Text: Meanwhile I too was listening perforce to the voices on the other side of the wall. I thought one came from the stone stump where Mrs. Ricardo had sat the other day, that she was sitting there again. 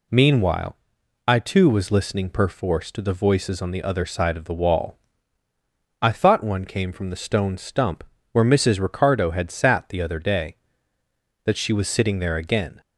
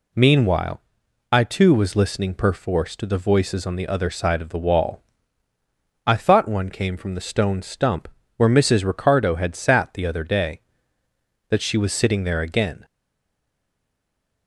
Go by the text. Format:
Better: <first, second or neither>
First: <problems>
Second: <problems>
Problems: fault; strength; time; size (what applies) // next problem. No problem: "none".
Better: first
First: pauses between "Meanwhile" and "I"; noticeable; at 0.7 s; 0.50 s long // pauses between "stump" and "where"; slight; at 8.0 s; 0.30 s long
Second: pauses between "Meanwhile" and "I"; noticeable; at 0.8 s; 0.50 s long // pauses between "stump" and "where"; slight; at 8.0 s; 0.30 s long // stays silent after the last word; noticeable; from 12.8 s on; 1.6 s long